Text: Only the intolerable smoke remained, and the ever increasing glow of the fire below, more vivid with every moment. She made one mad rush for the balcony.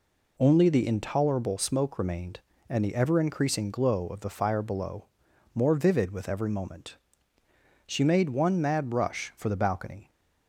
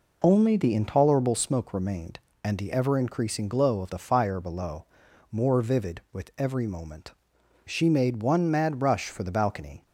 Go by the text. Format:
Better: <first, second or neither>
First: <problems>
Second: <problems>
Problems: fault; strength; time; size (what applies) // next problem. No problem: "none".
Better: neither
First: none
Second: none